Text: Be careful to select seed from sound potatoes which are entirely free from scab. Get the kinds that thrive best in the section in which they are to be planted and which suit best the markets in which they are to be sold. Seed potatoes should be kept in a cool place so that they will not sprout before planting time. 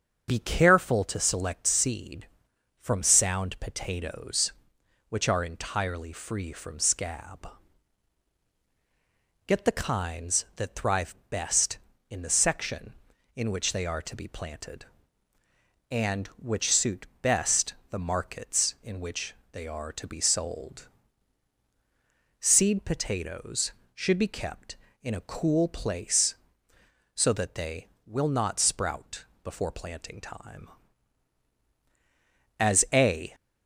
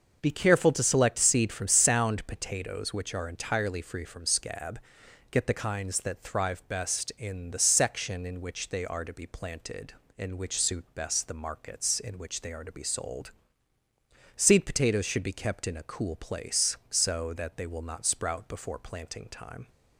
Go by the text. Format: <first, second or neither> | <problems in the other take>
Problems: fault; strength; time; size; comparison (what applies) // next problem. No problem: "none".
second | starts louder than the rest; until 1.3 s; 7 dB; also in the second // pauses between "thrive" and "best"; slight; at 11.1 s; 0.16 s long // pauses between "suit" and "best"; slight; at 17.0 s; 0.16 s long // pauses between "best" and "the"; slight; at 17.7 s; 0.16 s long // pauses between "which" and "they"; slight; at 19.3 s; 0.20 s long // pauses between "sprout" and "before"; slight; at 29.2 s; 0.20 s long // goes on to say "As a"; noticeable; from 32.5 s on; 0.76 s long